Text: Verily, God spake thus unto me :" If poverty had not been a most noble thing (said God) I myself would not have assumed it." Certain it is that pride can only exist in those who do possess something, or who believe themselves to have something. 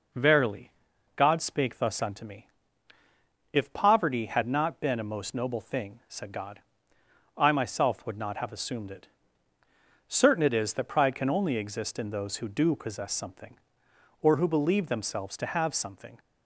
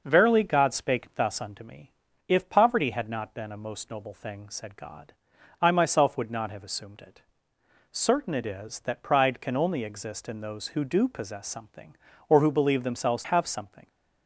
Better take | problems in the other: first | skips "to"; at 13.2 s

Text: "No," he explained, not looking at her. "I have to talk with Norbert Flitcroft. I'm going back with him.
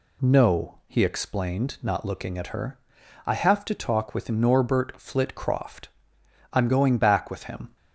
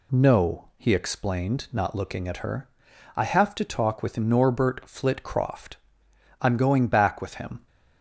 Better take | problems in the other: neither | none

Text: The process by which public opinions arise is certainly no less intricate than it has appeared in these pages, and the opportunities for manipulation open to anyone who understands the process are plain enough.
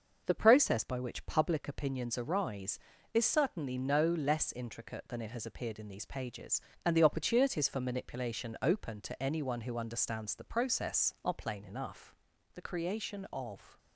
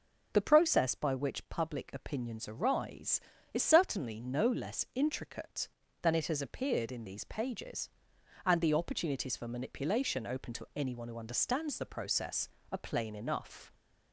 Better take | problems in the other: second | goes on to say "The creation of"; noticeable; from 12.5 s on; 1.2 s long

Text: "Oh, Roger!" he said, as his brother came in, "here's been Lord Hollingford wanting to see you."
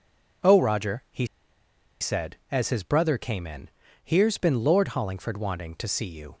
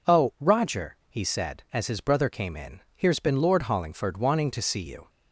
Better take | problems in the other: second | pauses between "he" and "said"; noticeable; at 1.2 s; 0.75 s long

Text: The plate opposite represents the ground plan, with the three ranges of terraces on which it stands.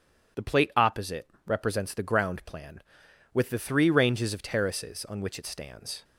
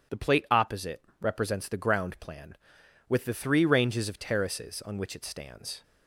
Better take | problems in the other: neither | pauses between "opposite" and "represents"; slight; the same in both

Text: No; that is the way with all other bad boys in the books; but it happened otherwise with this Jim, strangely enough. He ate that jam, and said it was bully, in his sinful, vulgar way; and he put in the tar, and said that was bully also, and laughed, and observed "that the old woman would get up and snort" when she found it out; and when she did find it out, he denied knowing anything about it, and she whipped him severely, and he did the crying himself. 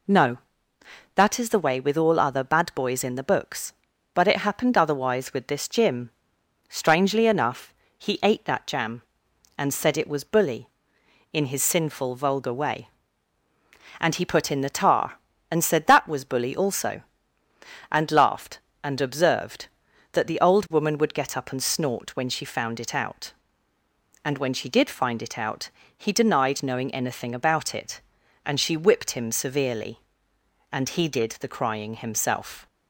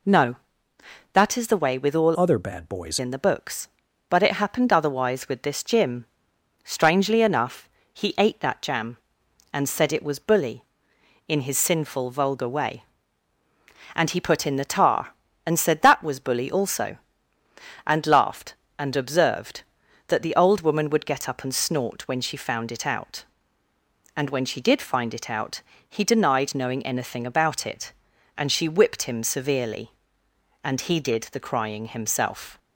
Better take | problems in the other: first | changes voice from "other" to "boys"; from 2.1 to 2.9 s; 0.8 s long

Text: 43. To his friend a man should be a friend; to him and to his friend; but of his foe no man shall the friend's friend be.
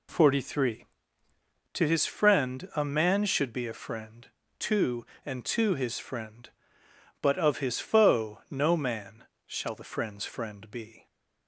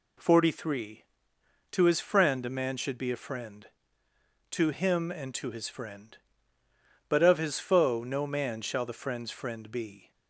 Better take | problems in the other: second | skips "him"; at 5.1 s // pauses between "man" and "shall"; slight; at 9.2 s; 0.22 s long

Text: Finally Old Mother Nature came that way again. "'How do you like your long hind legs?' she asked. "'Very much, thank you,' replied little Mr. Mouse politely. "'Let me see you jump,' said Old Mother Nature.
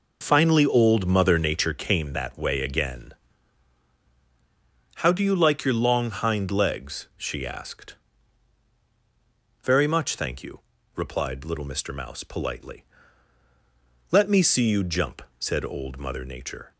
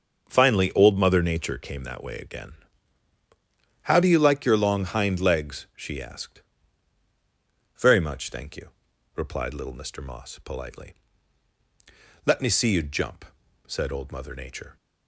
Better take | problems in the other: first | starts louder than the rest; until 1.2 s; 6.5 dB // says "Moss" for "Mouse"; at 9.9 s

